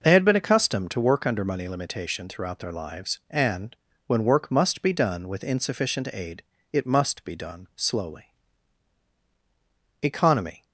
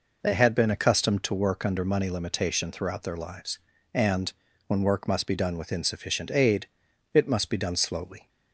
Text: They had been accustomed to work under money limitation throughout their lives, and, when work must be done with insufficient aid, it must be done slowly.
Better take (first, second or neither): second